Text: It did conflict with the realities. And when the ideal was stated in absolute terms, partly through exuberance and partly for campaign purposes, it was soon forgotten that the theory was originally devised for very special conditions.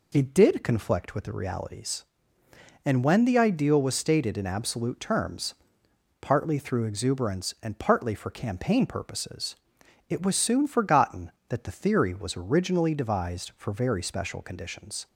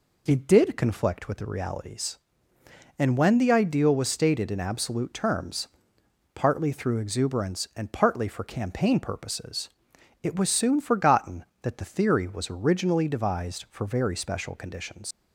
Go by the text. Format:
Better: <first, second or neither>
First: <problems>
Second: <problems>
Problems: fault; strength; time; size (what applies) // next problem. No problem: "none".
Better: first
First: none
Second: leaves "conditions" unfinished; at 15.1 s; 95 ms